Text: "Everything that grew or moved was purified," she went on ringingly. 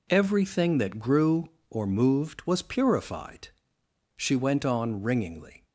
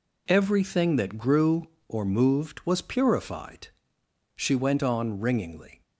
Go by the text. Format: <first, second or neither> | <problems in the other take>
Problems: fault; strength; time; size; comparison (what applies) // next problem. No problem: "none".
neither | none